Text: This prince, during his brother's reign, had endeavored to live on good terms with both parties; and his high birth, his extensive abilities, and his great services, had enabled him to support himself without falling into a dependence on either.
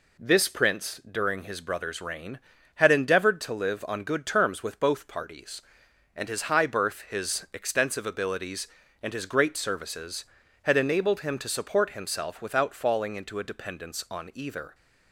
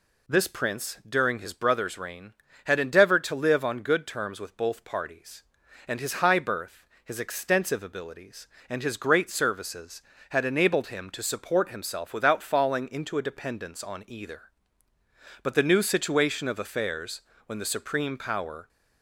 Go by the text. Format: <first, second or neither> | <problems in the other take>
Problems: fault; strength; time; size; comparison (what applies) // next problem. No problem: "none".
first | goes on to say "But the new situation of affairs when the supreme power"; strong; from 15.4 s on; 3.2 s long